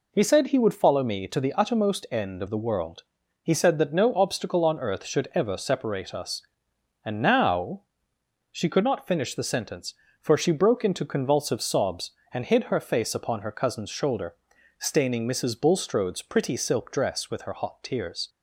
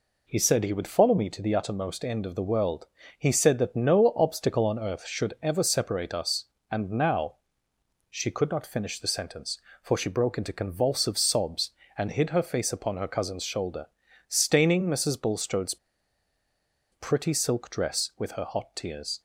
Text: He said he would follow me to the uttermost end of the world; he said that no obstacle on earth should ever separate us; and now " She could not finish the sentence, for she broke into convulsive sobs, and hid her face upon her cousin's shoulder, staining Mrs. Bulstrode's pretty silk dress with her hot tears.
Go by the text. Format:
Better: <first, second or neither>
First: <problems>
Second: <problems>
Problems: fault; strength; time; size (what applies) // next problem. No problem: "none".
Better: first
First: none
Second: pauses between "Bulstrode's" and "pretty"; at 15.7 s; 1.1 s long